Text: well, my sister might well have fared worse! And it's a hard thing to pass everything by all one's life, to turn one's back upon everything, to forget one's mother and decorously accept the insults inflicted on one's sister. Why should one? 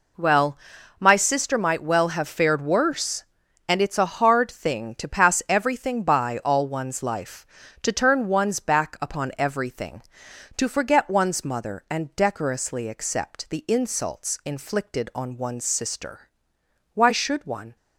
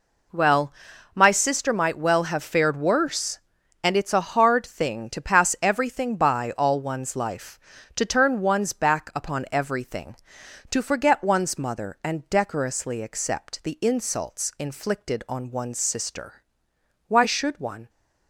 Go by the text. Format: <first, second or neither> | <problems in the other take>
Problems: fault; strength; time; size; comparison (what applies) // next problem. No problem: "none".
neither | none